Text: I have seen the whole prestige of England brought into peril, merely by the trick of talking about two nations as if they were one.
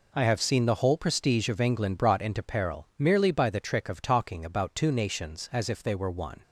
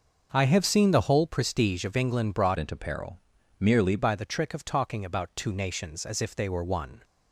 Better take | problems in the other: first | starts louder than the rest; until 1.3 s; 6 dB // changes voice from "into" to "merely"; from 2.5 to 3.9 s; 1.4 s long

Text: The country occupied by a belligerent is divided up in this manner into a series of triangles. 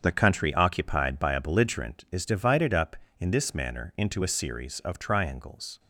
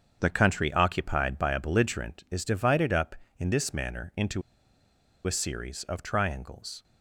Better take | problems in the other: first | starts louder than the rest; strong; until 1.2 s; 7.5 dB; strong in the first // pauses between "into" and "a"; noticeable; at 4.4 s; 0.85 s long

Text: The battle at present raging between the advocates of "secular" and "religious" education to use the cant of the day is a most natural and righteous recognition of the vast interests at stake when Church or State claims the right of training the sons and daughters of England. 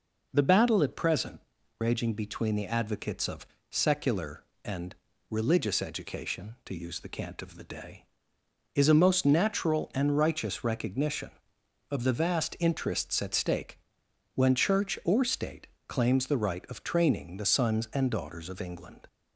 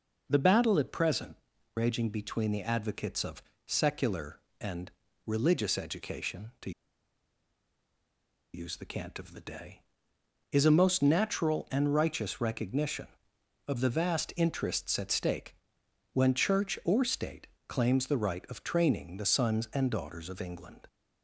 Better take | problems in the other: first | pauses between "present" and "raging"; at 1.3 s; 0.40 s long; also in the first // pauses between "of" and "secular"; slight; at 3.4 s; 0.24 s long; slight in the first // pauses between "and" and "religious"; slight; at 4.9 s; 0.36 s long; slight in the first // pauses between "to" and "use"; strong; at 6.7 s; 1.8 s long // pauses between "stake" and "when"; noticeable; at 15.5 s; 0.58 s long; noticeable in the first // pauses between "State" and "claims"; slight; at 17.4 s; 0.20 s long; slight in the first

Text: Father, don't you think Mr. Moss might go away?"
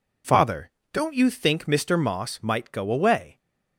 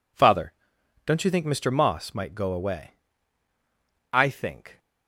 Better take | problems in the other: first | goes on to say "I think"; noticeable; from 4.1 s on; 0.66 s long

